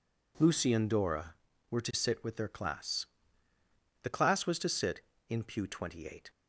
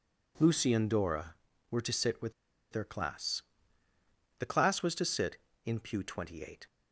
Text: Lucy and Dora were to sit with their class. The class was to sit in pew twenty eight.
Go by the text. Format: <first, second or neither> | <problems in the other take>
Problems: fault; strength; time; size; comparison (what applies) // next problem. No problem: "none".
first | pauses between "with" and "their"; at 2.3 s; 0.39 s long